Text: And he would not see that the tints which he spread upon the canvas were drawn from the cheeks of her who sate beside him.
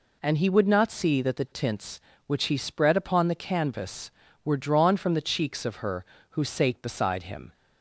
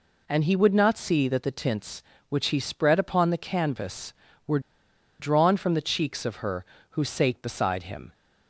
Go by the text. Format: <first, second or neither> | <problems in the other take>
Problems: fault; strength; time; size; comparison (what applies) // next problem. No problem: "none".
first | pauses between "were" and "drawn"; noticeable; at 4.5 s; 0.60 s long